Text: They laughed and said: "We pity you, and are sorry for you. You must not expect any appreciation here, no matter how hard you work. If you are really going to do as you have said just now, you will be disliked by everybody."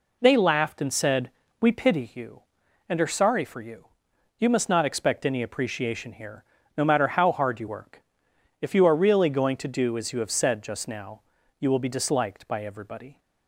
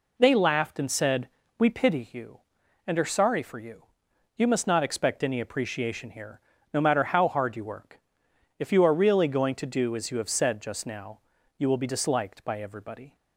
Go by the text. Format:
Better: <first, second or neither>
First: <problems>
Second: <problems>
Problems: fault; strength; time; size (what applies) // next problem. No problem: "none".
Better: neither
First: none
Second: none